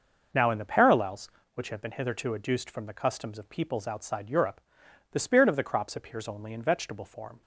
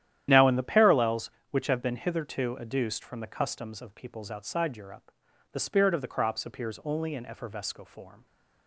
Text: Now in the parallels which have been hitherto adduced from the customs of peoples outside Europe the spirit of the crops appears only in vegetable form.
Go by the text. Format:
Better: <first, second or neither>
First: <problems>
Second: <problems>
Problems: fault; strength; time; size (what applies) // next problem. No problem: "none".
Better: first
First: pauses between "Europe" and "the"; noticeable; at 4.6 s; 0.50 s long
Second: starts louder than the rest; strong; until 1.3 s; 11 dB // pauses between "Europe" and "the"; at 5.0 s; 0.44 s long // says "effervesco" for "vegetable"; at 7.2 s